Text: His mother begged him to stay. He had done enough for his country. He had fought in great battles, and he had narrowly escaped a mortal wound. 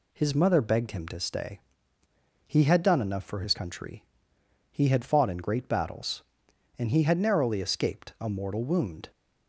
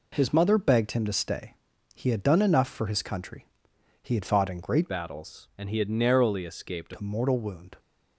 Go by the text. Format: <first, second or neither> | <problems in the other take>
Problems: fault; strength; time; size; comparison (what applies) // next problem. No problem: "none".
first | changes voice from "battles" to "escaped"; from 4.8 to 6.9 s; 2.1 s long